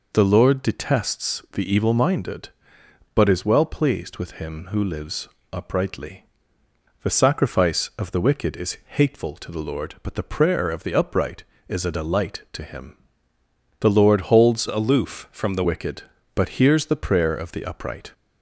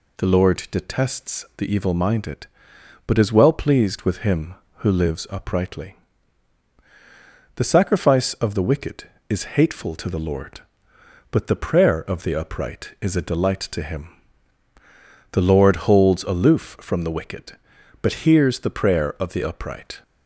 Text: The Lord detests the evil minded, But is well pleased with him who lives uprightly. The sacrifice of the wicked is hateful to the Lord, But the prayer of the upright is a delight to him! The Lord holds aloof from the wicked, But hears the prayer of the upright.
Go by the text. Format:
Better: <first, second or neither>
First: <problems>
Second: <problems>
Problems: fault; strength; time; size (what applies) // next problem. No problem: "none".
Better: second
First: pauses between "lives" and "uprightly"; slight; at 5.2 s; 0.28 s long // changes voice from "aloof" to "the"; from 14.6 to 15.6 s; 1.0 s long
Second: none